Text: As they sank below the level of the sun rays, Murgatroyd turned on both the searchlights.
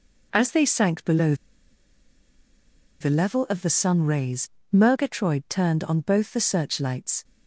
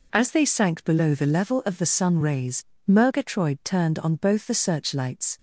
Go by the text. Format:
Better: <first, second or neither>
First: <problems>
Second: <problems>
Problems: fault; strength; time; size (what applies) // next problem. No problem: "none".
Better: second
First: pauses between "below" and "the"; strong; at 1.3 s; 1.6 s long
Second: none